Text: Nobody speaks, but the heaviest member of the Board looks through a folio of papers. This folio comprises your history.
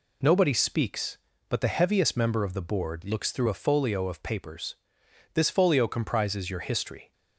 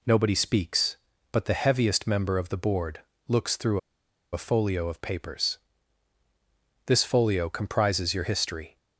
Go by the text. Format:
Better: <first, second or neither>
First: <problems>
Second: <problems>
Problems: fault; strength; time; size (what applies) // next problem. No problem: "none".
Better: first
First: none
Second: pauses between "Board" and "looks"; slight; at 3.0 s; 0.26 s long // pauses between "through" and "a"; noticeable; at 3.7 s; 0.55 s long